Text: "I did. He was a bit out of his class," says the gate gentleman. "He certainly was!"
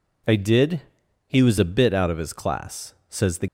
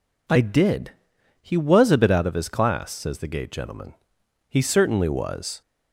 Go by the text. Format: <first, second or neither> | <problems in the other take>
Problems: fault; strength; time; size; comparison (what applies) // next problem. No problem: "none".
second | stops before "gate gentleman He certainly was"; at 3.4 s